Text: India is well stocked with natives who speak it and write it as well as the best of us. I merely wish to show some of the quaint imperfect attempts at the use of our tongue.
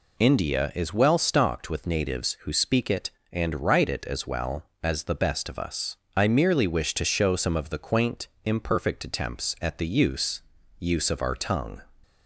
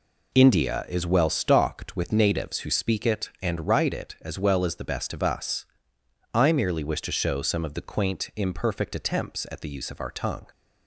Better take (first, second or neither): second